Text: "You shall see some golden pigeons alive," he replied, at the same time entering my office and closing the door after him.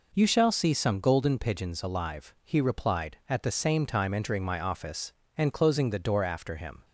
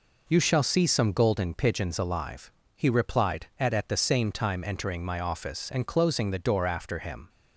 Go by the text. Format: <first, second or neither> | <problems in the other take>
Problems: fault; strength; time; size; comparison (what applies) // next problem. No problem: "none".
first | says "at" twice; at 3.7 s